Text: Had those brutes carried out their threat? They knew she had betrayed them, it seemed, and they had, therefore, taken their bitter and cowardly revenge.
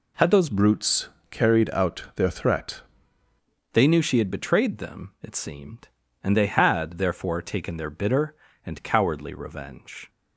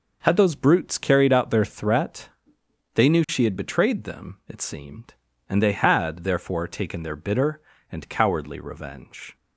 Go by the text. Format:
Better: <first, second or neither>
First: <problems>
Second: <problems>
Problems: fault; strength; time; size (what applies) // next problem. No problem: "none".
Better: second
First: changes voice from "brutes" to "threat"; from 0.4 to 2.8 s; 2.4 s long // pauses between "brutes" and "carried"; slight; at 1.0 s; 0.22 s long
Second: none